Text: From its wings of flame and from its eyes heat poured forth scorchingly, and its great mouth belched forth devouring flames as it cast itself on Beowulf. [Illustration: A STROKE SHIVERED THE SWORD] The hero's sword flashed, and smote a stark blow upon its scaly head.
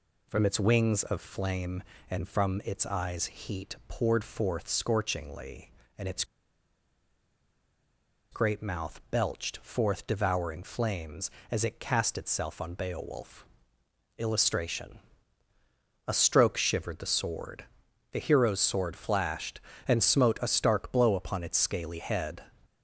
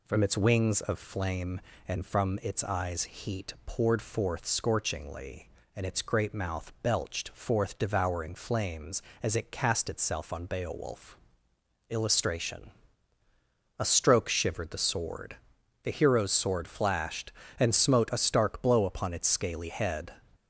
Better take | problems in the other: second | pauses between "its" and "great"; strong; at 6.2 s; 2.0 s long // pauses between "SWORD" and "The"; noticeable; at 17.6 s; 0.48 s long; noticeable in the second

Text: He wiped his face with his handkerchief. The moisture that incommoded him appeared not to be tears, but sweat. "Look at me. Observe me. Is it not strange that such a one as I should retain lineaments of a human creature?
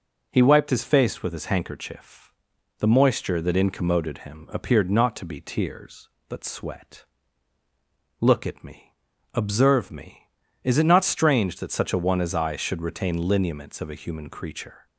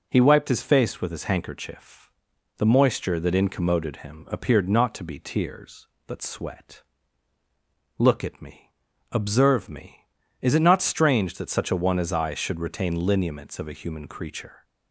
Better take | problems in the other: neither | none

